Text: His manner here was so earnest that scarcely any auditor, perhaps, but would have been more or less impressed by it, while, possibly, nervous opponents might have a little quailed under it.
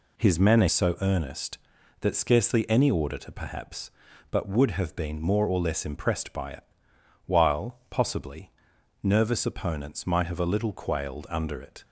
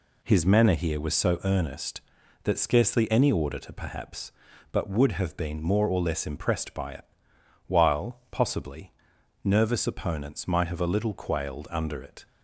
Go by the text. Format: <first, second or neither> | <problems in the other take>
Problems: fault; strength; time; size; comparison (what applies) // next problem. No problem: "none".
second | skips "here was"; at 0.6 s